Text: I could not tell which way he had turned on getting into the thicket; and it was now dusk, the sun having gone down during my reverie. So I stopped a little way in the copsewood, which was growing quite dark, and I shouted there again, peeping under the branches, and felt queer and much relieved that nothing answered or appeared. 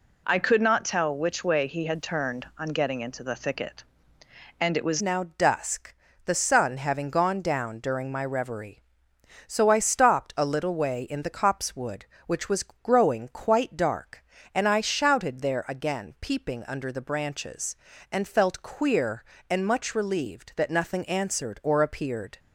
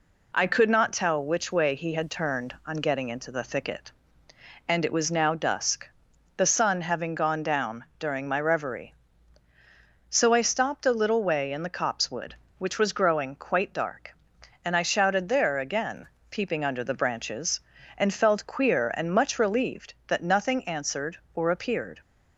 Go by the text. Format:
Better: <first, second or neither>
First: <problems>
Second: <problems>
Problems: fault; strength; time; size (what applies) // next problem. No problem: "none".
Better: second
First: changes voice at "now"; from 5.0 s on; 17.3 s long // pauses between "was" and "growing"; slight; at 12.6 s; 0.18 s long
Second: none